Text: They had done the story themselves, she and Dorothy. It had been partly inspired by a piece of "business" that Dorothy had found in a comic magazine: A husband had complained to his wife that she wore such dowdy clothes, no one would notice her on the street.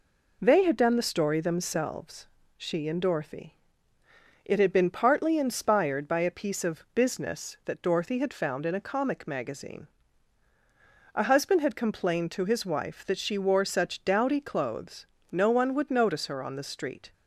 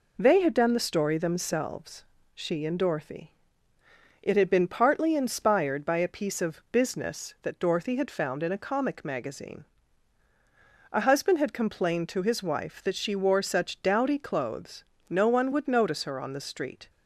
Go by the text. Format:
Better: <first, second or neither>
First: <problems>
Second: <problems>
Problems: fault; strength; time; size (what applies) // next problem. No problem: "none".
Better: neither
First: none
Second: none